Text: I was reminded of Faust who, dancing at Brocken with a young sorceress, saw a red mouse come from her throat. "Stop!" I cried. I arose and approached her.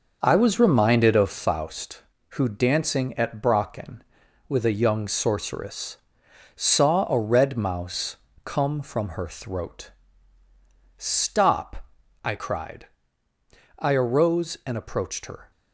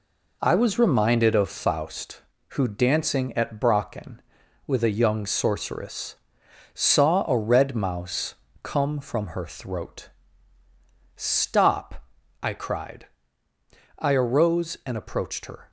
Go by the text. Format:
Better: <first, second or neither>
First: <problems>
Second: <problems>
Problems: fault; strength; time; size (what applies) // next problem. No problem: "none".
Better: second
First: starts louder than the rest; until 1.4 s; 6 dB // pauses between "mouse" and "come"; slight; at 8.1 s; 0.26 s long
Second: pauses between "mouse" and "come"; slight; at 8.3 s; 0.26 s long